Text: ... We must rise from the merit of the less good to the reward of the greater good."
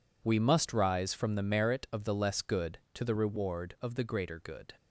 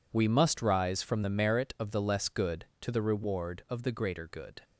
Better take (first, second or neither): neither